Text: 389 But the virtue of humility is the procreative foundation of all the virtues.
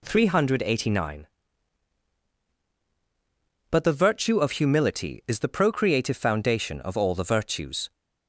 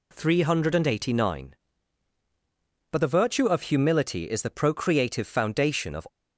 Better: first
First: none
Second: stops before "all the virtues"; at 6.0 s

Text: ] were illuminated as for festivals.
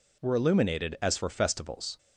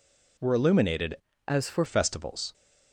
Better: first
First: none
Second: changes voice from "as" to "for"; from 1.4 to 1.8 s; 0.4 s long

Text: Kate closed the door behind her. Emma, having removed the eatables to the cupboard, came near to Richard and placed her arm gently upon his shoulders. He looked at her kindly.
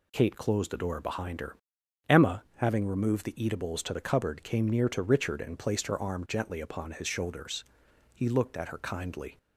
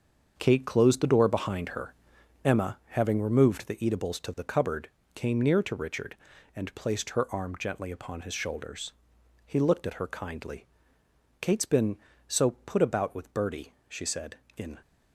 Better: first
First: none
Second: starts louder than the rest; until 1.3 s; 7 dB // goes on to say "Kate's been so put about with Bertie she said in"; strong; from 11.4 s on; 3.3 s long

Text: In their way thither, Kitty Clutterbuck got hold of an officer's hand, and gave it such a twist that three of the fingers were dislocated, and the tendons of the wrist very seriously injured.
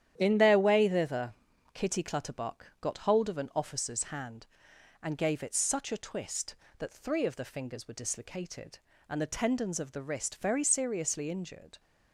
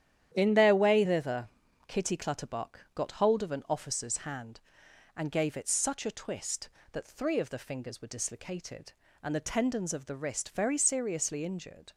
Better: neither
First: starts louder than the rest; strong; until 1.1 s; 10 dB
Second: starts louder than the rest; strong; until 1.3 s; 10 dB

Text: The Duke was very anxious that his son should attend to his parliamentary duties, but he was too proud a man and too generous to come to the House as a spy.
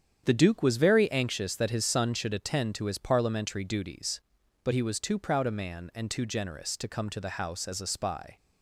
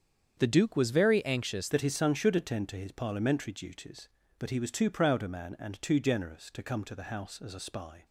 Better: first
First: starts louder than the rest; strong; until 1.2 s; 8.5 dB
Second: starts louder than the rest; strong; until 1.3 s; 7.5 dB // changes voice at "that"; from 1.7 s on; 6.3 s long

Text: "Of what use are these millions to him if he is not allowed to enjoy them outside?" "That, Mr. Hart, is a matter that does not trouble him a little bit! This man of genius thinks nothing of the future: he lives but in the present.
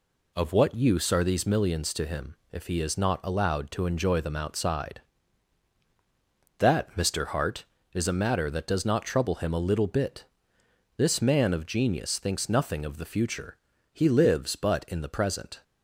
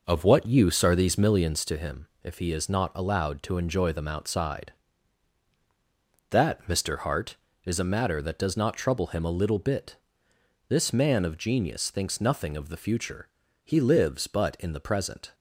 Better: first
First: pauses between "him" and "if"; slight; at 2.3 s; 0.18 s long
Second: starts louder than the rest; noticeable; until 1.8 s; 5.5 dB // pauses between "him" and "if"; slight; at 2.0 s; 0.18 s long

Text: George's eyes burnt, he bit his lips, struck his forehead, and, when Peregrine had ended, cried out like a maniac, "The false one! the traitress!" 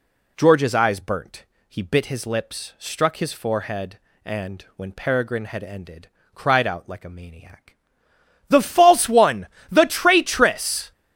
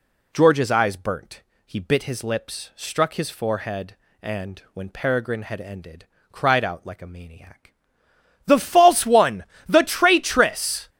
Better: neither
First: none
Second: none

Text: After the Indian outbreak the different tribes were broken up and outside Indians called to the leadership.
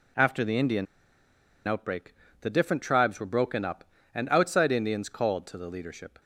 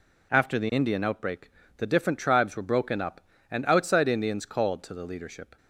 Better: second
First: pauses between "Indian" and "outbreak"; noticeable; at 0.8 s; 0.82 s long // pauses between "outbreak" and "the"; slight; at 2.1 s; 0.26 s long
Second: pauses between "outbreak" and "the"; slight; at 1.5 s; 0.26 s long

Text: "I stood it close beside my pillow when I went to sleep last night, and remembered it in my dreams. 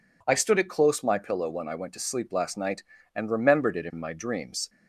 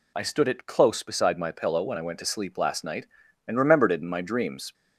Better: second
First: skips "beside"; at 1.0 s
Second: none

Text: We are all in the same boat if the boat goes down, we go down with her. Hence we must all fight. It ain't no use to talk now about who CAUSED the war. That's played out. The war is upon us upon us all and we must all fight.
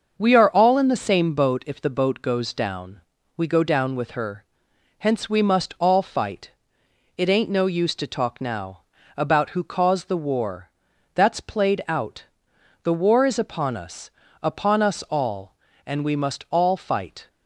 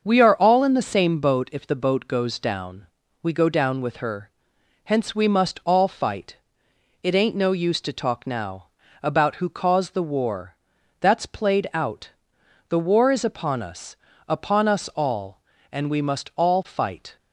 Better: neither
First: starts louder than the rest; until 1.1 s; 6.5 dB // pauses between "now" and "about"; slight; at 8.8 s; 0.34 s long // pauses between "us" and "upon"; slight; at 14.0 s; 0.34 s long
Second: starts louder than the rest; until 1.0 s; 6.5 dB // pauses between "now" and "about"; slight; at 8.6 s; 0.34 s long // pauses between "us" and "upon"; slight; at 13.9 s; 0.34 s long

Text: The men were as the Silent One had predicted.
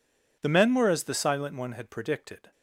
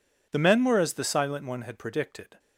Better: neither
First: none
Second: none

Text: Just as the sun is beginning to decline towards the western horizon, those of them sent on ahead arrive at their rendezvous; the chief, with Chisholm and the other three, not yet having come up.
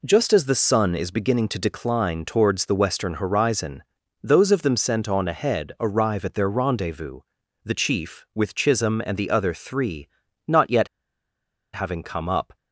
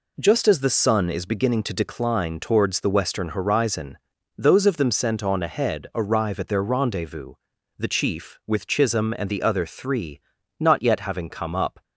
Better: second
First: pauses between "yet" and "having"; noticeable; at 10.8 s; 0.86 s long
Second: none

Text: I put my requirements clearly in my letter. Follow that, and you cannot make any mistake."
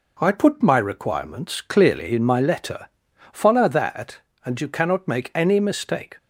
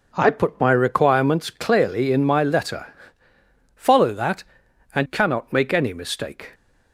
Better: first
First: none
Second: skips "you"; at 5.0 s

